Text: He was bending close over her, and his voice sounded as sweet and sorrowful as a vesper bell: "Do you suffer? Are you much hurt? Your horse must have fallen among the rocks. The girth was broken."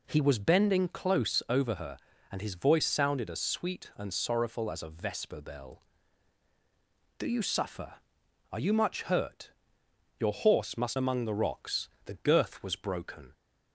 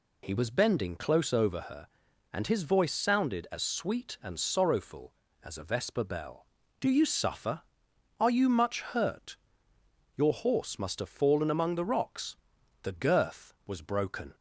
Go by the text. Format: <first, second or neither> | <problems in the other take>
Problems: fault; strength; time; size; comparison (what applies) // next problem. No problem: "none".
second | skips "have fallen"; at 10.9 s